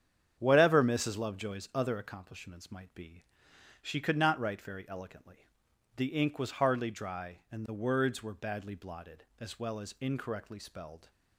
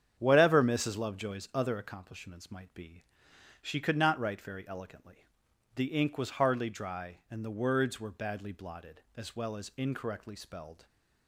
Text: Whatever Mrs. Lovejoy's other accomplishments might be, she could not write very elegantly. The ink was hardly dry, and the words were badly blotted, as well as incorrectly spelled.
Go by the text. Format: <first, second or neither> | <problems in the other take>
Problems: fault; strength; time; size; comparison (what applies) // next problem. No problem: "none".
neither | starts louder than the rest; strong; the same in both